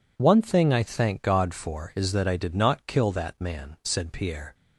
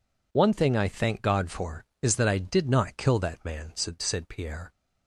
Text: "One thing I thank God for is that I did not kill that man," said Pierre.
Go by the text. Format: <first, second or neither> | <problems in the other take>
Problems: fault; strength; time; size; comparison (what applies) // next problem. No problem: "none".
first | says "said" twice; at 4.0 s